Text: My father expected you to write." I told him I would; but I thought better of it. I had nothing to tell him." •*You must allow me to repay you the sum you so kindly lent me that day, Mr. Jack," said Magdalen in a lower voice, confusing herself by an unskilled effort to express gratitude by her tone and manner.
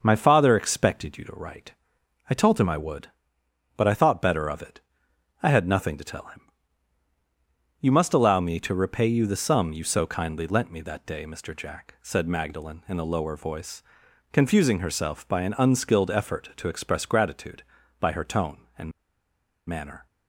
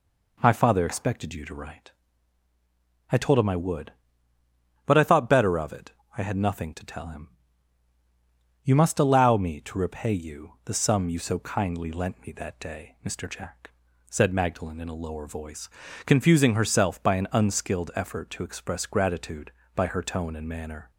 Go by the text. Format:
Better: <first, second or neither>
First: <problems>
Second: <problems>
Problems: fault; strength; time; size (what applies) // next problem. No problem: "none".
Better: second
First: starts louder than the rest; noticeable; until 1.0 s; 6 dB // pauses between "and" and "manner"; noticeable; at 18.9 s; 0.78 s long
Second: none